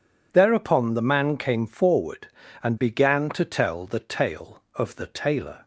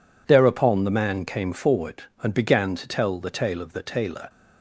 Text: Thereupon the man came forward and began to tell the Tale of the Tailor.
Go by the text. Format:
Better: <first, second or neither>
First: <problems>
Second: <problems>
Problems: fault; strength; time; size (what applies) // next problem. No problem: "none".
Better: neither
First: none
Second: none